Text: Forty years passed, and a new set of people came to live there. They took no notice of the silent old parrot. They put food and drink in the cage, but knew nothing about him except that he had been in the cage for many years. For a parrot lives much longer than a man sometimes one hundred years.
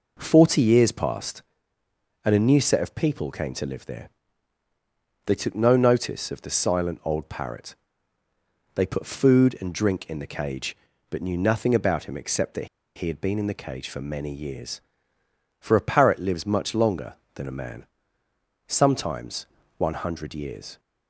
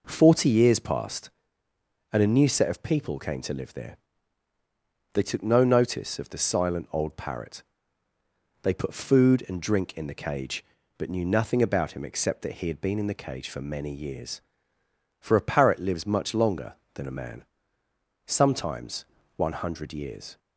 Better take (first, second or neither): second